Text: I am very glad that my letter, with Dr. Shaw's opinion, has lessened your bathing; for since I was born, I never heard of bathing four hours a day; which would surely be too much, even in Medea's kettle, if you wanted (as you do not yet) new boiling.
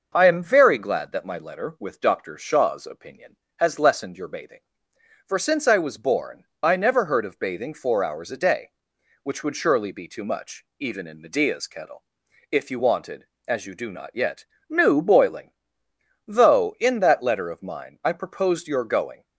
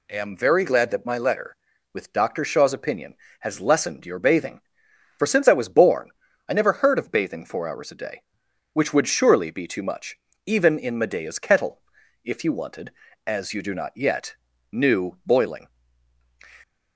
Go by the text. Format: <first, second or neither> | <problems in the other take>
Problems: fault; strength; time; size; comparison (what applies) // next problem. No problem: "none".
second | goes on to say "Though in that letter of mine I proposed your going"; strong; from 16.2 s on; 2.9 s long